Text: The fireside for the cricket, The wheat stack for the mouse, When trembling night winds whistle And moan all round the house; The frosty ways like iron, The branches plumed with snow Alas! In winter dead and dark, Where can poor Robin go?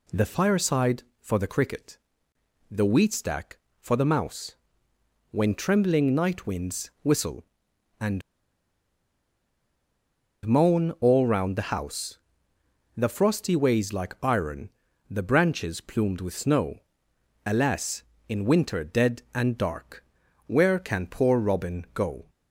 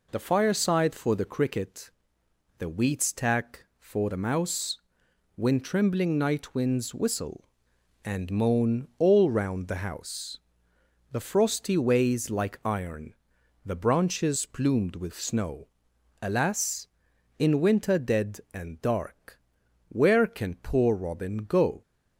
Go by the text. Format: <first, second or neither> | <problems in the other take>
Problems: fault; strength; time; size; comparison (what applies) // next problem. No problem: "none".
second | pauses between "And" and "moan"; strong; at 8.2 s; 2.2 s long // pauses between "snow" and "Alas"; noticeable; at 16.8 s; 0.66 s long; noticeable in the second